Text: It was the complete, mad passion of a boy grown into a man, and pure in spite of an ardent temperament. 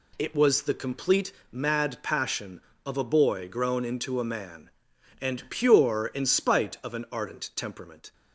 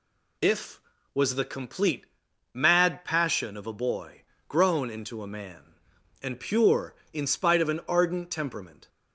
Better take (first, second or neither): first